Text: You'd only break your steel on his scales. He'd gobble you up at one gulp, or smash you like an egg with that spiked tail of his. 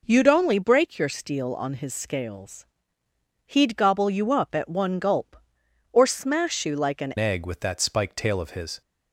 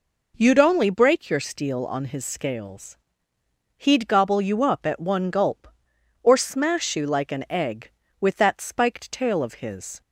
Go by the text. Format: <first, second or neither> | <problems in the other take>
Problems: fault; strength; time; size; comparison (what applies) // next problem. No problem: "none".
second | changes voice at "egg"; from 7.1 s on; 1.7 s long